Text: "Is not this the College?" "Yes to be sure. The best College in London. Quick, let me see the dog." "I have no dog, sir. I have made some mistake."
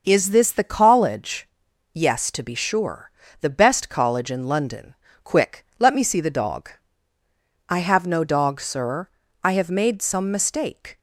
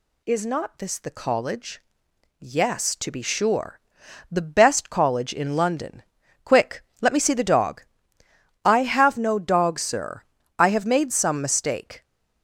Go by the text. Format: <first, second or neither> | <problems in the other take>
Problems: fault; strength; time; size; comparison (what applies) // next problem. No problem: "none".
second | skips "not"; at 0.2 s